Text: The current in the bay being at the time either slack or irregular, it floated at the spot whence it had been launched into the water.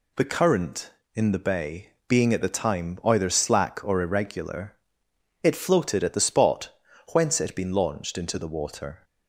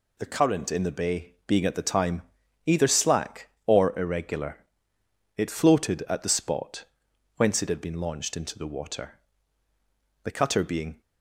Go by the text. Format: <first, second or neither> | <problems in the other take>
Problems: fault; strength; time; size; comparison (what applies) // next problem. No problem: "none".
first | pauses between "time" and "either"; at 2.2 s; 0.42 s long // pauses between "spot" and "whence"; noticeable; at 6.8 s; 0.52 s long; also in the first // goes on to say "The cutter being"; noticeable; from 10.2 s on; 0.76 s long